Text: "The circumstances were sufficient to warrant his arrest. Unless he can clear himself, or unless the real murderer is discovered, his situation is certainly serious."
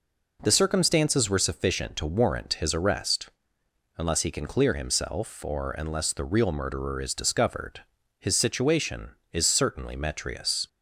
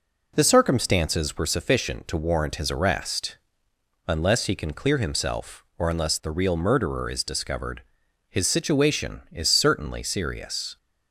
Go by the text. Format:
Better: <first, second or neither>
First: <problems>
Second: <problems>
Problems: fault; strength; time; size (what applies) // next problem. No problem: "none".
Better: second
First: says "metrius" for "serious"; at 9.9 s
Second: none